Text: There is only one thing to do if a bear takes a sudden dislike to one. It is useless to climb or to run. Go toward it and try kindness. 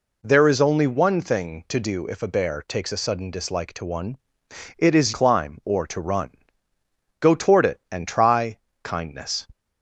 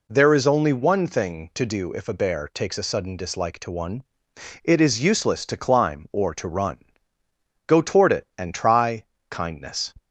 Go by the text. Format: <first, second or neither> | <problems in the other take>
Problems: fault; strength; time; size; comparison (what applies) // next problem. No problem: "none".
second | skips "useless to"; at 5.1 s // pauses between "try" and "kindness"; slight; at 8.5 s; 0.24 s long; slight in the second